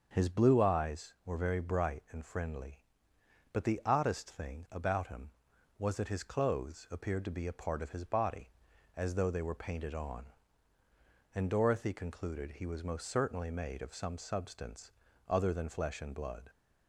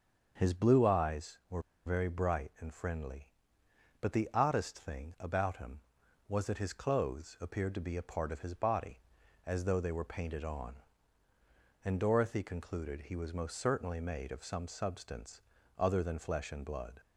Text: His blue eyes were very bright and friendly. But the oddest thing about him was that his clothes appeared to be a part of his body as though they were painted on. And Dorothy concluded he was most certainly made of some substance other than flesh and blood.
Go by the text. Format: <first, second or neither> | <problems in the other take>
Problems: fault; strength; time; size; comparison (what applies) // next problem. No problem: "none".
first | starts louder than the rest; until 1.3 s; 6.5 dB; also in the first // pauses between "were" and "very"; slight; at 1.6 s; 0.24 s long // pauses between "substance" and "other"; at 15.4 s; 0.38 s long; also in the first